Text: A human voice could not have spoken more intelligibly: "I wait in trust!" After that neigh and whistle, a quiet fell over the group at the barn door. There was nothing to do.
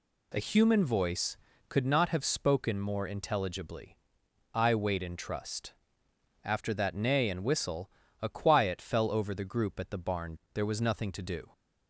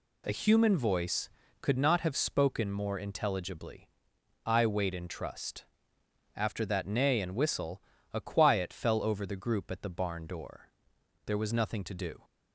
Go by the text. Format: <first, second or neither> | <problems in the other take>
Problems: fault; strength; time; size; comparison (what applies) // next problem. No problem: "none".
second | skips "door"; at 10.4 s